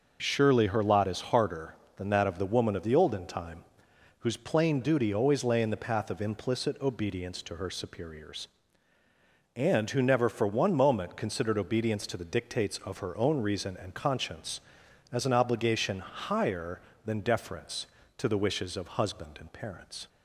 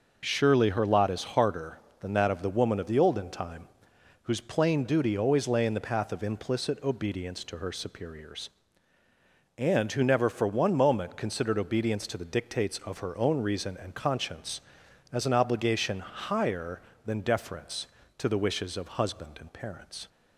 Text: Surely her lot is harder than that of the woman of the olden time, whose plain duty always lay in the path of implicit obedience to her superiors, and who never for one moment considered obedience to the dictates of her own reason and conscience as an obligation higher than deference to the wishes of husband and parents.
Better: neither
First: none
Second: none

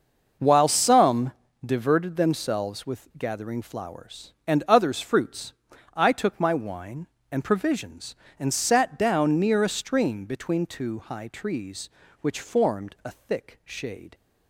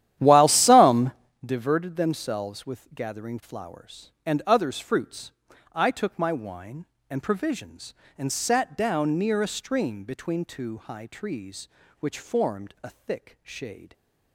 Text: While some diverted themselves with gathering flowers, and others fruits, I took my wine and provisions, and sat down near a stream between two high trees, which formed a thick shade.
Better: first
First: pauses between "some" and "diverted"; slight; at 1.3 s; 0.32 s long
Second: starts louder than the rest; strong; until 1.4 s; 11.5 dB // pauses between "some" and "diverted"; slight; at 1.1 s; 0.32 s long

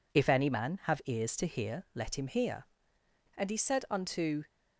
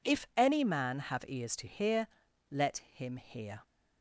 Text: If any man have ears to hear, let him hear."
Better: second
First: goes on to say "And he said unto"; noticeable; from 3.3 s on; 1.0 s long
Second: none

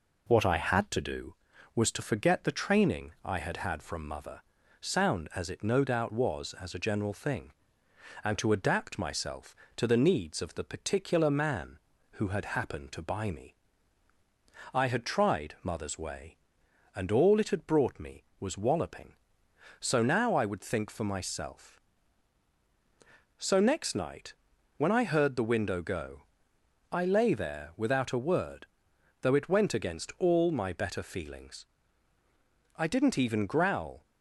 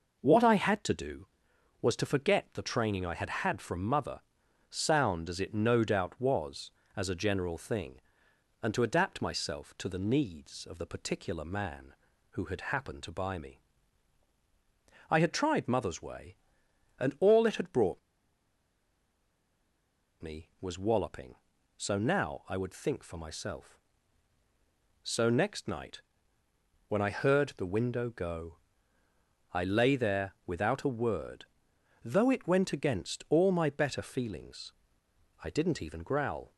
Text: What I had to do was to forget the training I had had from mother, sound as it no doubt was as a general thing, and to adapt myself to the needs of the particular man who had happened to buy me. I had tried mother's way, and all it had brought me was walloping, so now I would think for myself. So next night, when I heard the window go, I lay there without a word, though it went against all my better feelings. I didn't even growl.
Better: first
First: none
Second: pauses between "brought" and "me"; strong; at 17.9 s; 2.2 s long

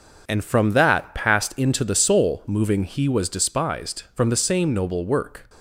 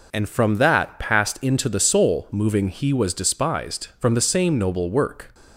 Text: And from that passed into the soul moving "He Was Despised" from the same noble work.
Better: second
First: gets quieter; strong; throughout; 8 dB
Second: none

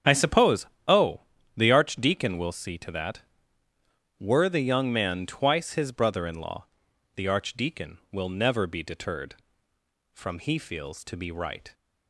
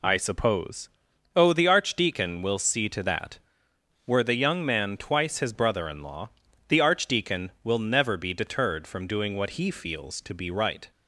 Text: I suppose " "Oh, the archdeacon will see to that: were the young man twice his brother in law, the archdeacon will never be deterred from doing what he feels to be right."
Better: second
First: starts louder than the rest; strong; until 1.1 s; 7.5 dB // skips "doing what"; at 10.3 s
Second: none

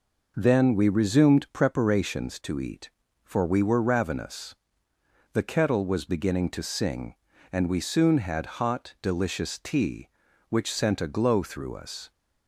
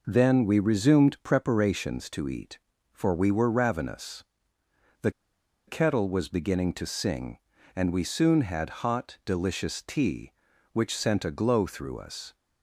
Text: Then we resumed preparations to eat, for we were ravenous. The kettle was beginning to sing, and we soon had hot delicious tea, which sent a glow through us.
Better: first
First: none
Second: pauses between "The" and "kettle"; noticeable; at 5.0 s; 0.57 s long

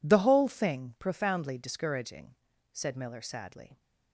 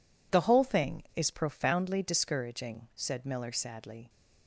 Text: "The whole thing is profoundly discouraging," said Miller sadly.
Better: second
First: skips "is"; at 0.9 s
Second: none

